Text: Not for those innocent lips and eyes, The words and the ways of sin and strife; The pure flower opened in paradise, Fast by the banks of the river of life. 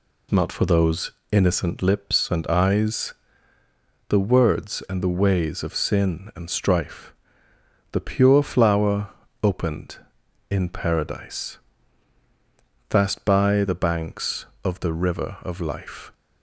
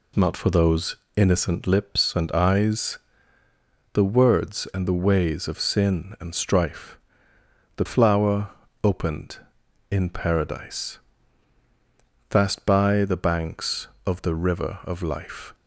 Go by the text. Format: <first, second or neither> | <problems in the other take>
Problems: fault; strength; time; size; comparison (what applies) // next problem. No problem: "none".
first | pauses between "those" and "innocent"; slight; at 0.9 s; 0.20 s long; slight in the first // skips "pure"; at 7.8 s // pauses between "flower" and "opened"; slight; at 8.5 s; 0.32 s long; slight in the first